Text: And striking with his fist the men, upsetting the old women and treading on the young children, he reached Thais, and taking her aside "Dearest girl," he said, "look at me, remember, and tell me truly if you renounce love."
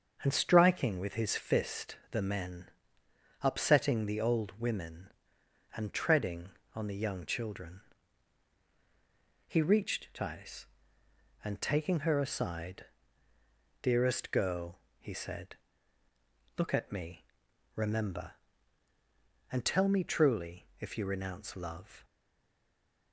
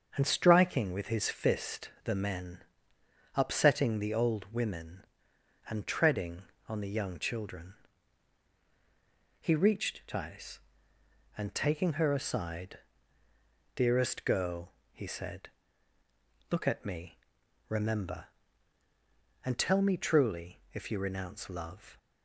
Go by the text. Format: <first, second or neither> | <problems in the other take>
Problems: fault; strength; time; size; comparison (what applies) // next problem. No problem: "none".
second | starts louder than the rest; until 1.2 s; 6.5 dB; also in the second // pauses between "aside" and "Dearest"; noticeable; at 12.8 s; 0.94 s long; noticeable in the second // stays silent after the last word; from 22.0 s on; 1.1 s long